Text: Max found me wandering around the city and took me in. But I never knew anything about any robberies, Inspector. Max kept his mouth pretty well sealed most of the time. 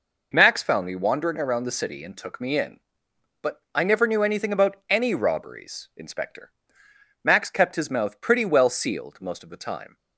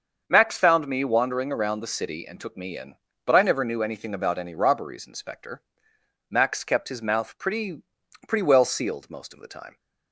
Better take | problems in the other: first | starts louder than the rest; until 1.2 s; 6.5 dB // says "pretty" twice; at 8.2 s

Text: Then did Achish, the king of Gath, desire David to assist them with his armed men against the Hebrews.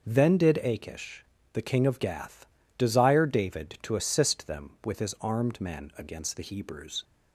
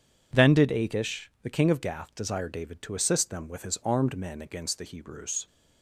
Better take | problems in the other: neither | none

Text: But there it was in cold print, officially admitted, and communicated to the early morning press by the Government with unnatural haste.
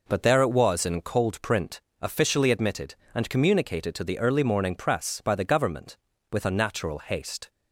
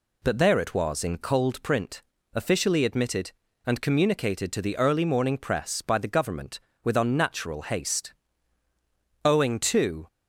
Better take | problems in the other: first | goes on to say "Owing to"; noticeable; from 9.2 s on; 0.82 s long

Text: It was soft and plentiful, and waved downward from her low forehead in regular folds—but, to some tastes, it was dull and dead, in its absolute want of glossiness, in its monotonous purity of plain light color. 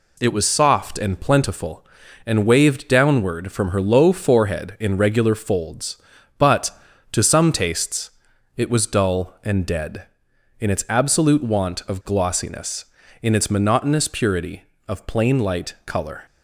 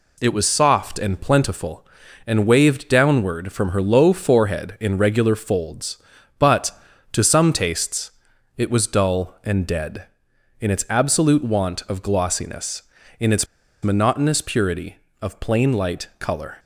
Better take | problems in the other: first | pauses between "its" and "monotonous"; at 13.4 s; 0.36 s long

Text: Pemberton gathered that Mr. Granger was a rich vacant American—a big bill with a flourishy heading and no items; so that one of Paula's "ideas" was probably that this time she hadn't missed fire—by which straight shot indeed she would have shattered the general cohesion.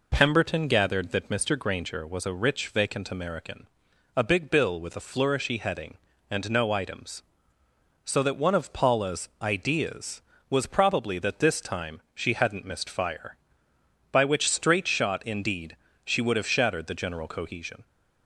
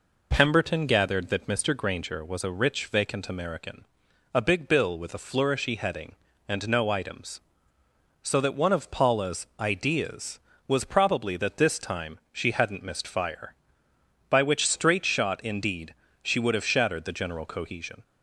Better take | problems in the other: neither | pauses between "indeed" and "she"; slight; the same in both

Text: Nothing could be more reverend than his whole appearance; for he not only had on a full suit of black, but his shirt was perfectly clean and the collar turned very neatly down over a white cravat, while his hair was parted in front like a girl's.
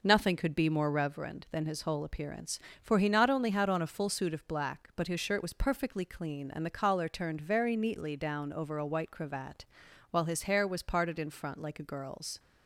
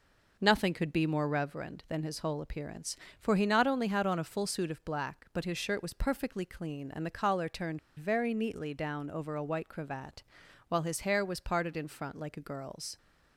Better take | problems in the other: first | pauses between "turned" and "very"; slight; at 7.7 s; 0.19 s long

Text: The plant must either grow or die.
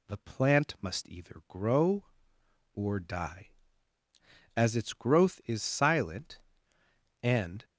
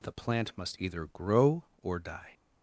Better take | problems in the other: second | goes on to say "As its growth is silent and"; strong; from 4.5 s on; 3.0 s long

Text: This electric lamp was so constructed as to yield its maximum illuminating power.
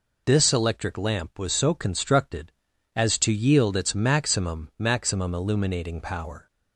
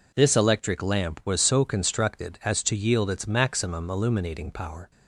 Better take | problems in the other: second | says "maximum" twice; at 4.7 s

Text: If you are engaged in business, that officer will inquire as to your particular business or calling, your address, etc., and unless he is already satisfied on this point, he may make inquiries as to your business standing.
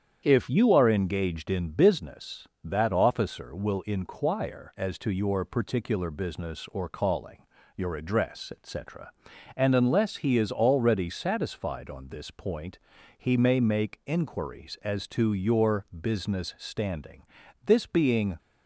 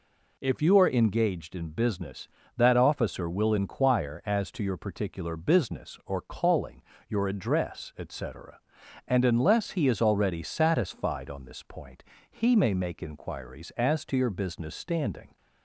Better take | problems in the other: second | starts louder than the rest; strong; until 1.2 s; 8.5 dB // goes on to say "This being"; noticeable; from 17.6 s on; 0.72 s long

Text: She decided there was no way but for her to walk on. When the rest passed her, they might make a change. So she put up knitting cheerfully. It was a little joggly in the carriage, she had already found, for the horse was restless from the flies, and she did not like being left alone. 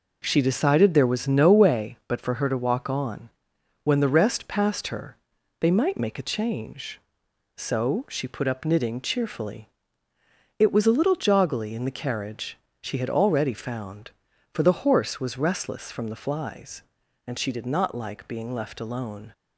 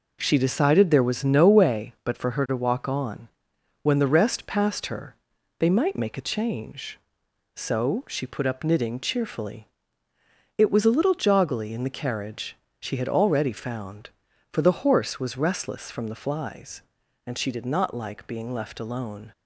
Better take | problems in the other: neither | none

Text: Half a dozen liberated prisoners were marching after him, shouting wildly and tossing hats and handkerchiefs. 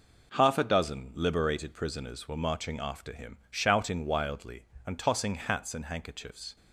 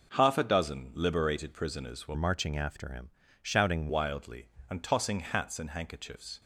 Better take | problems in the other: first | changes voice from "marching" to "shouting"; from 2.1 to 3.8 s; 1.7 s long

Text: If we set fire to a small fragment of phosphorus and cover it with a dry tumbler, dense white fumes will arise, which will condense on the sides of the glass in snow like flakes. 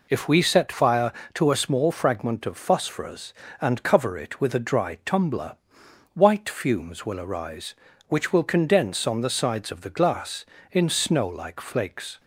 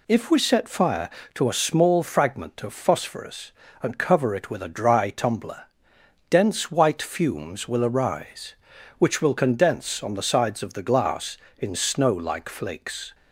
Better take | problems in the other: second | skips "dense"; at 5.8 s

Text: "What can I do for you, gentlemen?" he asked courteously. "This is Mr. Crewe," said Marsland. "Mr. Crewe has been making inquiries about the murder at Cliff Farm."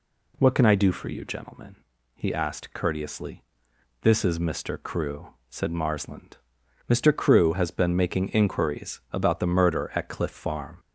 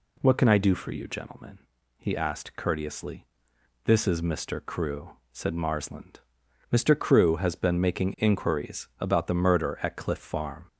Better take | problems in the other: neither | none

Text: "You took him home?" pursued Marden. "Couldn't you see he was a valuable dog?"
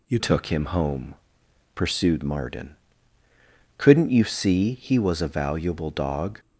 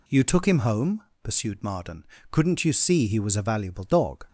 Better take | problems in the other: second | changes voice at "took"; from 0.1 s on; 6.2 s long

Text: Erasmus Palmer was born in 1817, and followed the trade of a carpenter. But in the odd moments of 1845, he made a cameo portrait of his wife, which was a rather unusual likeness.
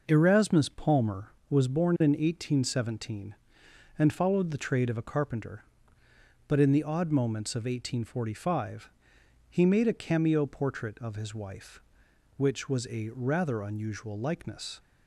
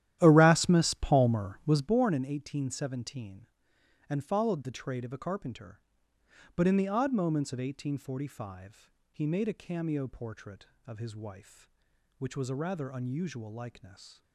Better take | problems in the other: first | starts louder than the rest; strong; until 2.0 s; 12.5 dB

